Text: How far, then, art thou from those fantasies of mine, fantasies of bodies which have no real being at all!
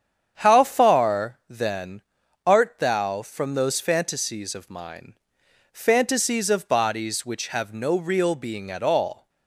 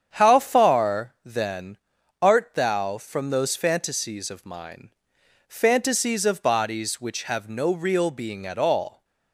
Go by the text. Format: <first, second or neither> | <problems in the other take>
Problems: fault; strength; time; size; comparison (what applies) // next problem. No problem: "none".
neither | starts louder than the rest; strong; the same in both